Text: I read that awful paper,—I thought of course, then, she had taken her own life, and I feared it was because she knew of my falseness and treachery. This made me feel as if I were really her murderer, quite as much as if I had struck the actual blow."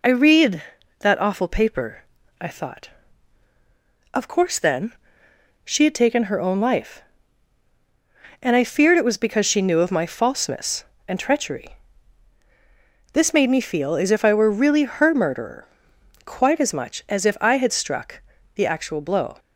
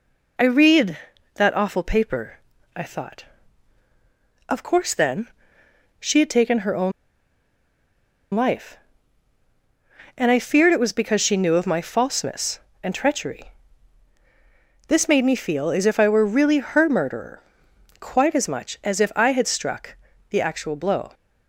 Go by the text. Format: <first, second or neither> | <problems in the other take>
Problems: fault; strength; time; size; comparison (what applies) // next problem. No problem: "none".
first | pauses between "own" and "life"; strong; at 6.9 s; 1.4 s long // pauses between "struck" and "the"; slight; at 19.9 s; 0.34 s long; slight in the first